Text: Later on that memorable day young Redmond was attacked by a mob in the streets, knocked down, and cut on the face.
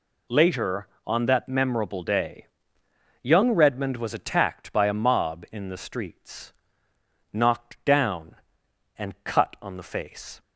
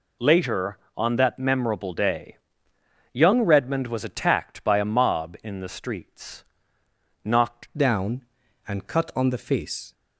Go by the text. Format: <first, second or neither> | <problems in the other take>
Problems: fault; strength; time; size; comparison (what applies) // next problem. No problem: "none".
first | pauses between "day" and "young"; noticeable; at 2.3 s; 0.76 s long; noticeable in the first // changes voice at "down"; from 7.7 s on; 2.2 s long